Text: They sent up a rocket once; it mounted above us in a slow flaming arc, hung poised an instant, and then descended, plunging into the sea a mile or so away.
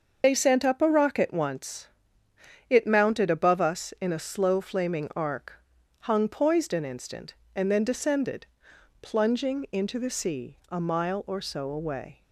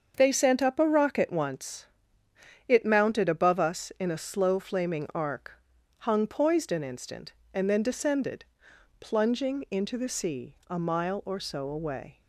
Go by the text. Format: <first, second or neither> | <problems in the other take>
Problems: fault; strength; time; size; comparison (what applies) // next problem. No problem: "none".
second | loses the start of "They"; at 0.2 s; 75 ms // starts louder than the rest; until 1.2 s; 6.5 dB; also in the second